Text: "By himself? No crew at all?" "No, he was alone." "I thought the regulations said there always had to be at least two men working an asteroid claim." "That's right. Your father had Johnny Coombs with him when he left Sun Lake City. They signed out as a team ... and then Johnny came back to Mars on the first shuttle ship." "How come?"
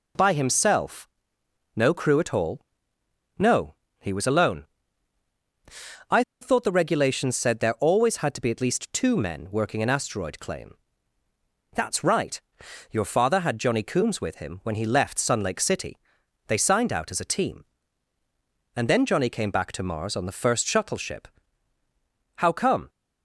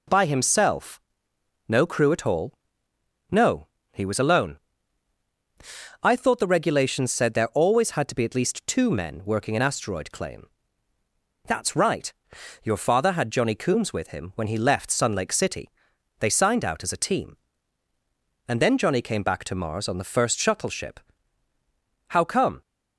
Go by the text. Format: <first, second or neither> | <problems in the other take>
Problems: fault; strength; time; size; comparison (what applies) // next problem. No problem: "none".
second | pauses between "I" and "thought"; slight; at 6.2 s; 0.17 s long